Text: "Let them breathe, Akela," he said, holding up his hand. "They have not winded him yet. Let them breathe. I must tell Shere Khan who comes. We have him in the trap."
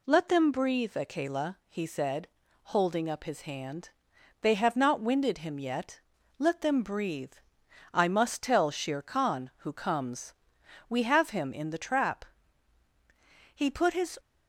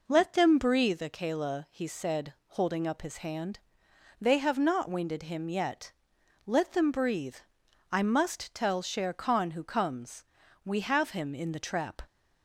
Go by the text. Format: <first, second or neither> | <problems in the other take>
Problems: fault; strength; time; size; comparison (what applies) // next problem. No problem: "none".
second | goes on to say "He put his"; noticeable; from 13.5 s on; 0.64 s long